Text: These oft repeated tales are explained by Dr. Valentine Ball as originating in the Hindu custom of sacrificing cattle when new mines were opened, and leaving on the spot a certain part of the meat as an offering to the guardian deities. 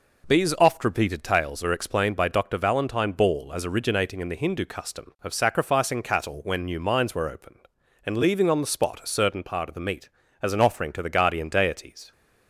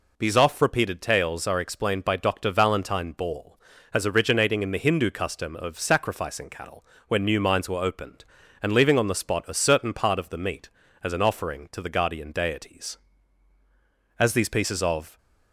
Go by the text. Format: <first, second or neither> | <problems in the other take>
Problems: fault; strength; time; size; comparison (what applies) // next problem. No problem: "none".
first | pauses between "cattle" and "when"; slight; at 6.8 s; 0.22 s long // goes on to say "As these pieces of"; noticeable; from 14.1 s on; 1.0 s long